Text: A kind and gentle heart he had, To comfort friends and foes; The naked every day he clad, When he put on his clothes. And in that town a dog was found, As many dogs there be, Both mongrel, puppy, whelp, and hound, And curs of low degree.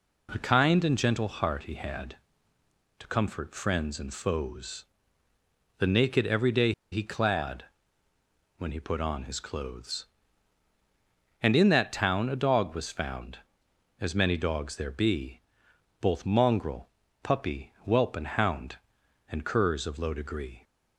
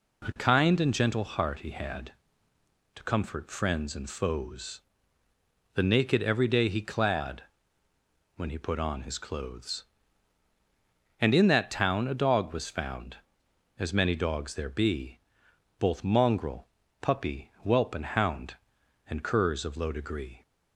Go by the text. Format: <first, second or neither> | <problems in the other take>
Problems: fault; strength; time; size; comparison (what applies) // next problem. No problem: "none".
second | pauses between "day" and "he"; slight; at 6.7 s; 0.19 s long